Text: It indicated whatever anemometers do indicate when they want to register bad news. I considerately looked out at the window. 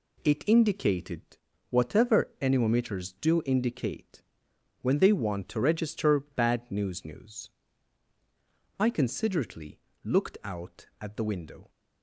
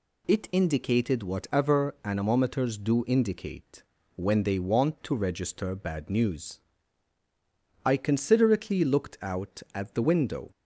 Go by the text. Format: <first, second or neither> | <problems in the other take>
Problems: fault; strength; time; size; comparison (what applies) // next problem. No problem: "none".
second | pauses between "indicated" and "whatever"; noticeable; at 1.2 s; 0.50 s long // pauses between "indicate" and "when"; noticeable; at 4.2 s; 0.60 s long; slight in the second // says "news" twice; at 7.0 s // pauses between "considerately" and "looked"; slight; at 9.7 s; 0.26 s long